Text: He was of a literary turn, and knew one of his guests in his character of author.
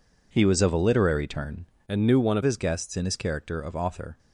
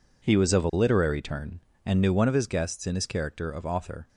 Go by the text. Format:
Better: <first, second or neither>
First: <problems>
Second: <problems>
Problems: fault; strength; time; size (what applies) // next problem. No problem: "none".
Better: second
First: changes voice from "and" to "of"; from 1.8 to 2.4 s; 0.6 s long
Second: none